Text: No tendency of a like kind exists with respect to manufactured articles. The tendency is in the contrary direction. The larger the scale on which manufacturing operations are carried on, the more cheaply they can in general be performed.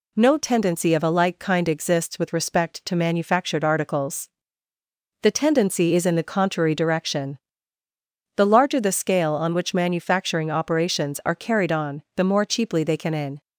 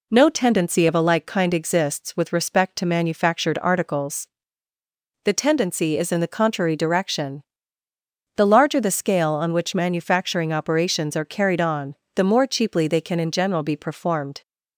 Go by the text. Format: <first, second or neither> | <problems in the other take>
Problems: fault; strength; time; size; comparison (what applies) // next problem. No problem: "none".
second | stops before "general be performed"; at 13.4 s